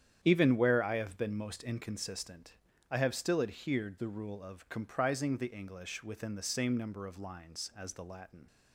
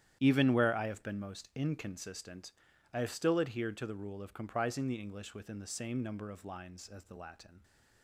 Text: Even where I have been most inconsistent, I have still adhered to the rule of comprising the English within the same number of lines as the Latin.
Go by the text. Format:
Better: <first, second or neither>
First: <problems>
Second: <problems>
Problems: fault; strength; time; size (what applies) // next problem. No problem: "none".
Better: second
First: starts louder than the rest; strong; until 1.2 s; 9.5 dB // skips "to"; at 3.9 s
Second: starts louder than the rest; strong; until 1.2 s; 11 dB